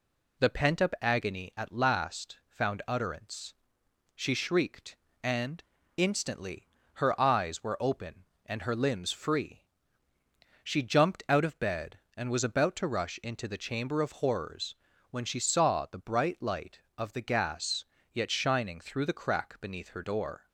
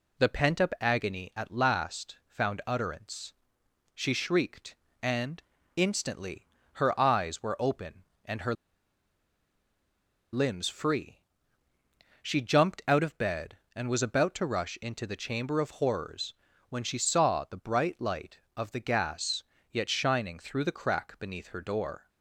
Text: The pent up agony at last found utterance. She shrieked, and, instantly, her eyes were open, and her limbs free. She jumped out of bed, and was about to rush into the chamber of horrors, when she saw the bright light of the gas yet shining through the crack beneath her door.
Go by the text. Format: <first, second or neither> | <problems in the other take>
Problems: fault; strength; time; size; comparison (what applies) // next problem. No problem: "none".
first | pauses between "her" and "limbs"; strong; at 8.5 s; 1.7 s long // pauses between "gas" and "yet"; slight; at 19.4 s; 0.26 s long; slight in the first